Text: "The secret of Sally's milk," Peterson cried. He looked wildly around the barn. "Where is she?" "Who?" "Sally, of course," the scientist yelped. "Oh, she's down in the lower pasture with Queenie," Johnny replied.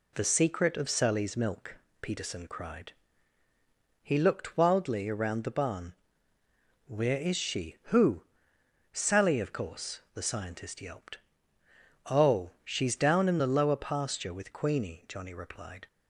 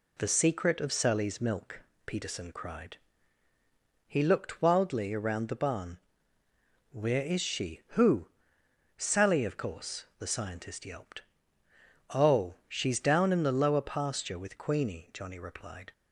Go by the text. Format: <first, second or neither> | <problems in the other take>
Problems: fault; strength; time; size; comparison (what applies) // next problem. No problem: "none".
neither | none